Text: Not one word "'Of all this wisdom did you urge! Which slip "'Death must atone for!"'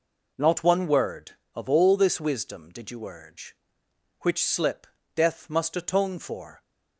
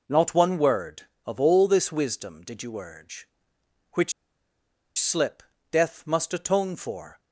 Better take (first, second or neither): first